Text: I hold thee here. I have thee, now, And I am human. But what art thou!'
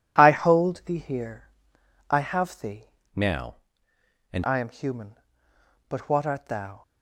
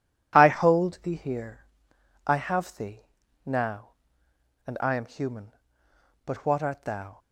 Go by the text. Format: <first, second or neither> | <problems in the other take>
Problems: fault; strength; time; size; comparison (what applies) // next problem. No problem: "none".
second | changes voice from "now" to "And"; from 3.1 to 4.4 s; 1.3 s long